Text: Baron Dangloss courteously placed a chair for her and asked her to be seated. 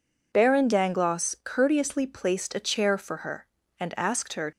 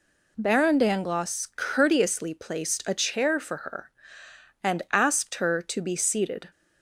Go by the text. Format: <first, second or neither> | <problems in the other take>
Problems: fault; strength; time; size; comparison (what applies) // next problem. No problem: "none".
second | stops before "to be seated"; at 4.5 s